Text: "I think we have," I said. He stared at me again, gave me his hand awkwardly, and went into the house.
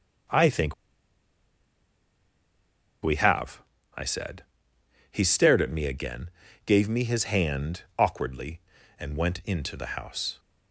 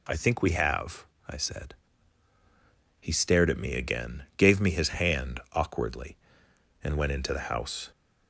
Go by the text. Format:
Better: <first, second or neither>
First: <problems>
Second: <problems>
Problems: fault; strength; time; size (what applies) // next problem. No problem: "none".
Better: second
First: starts louder than the rest; until 3.6 s; 6.5 dB // pauses between "think" and "we"; strong; at 0.7 s; 2.2 s long // pauses between "hand" and "awkwardly"; slight; at 7.8 s; 0.16 s long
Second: none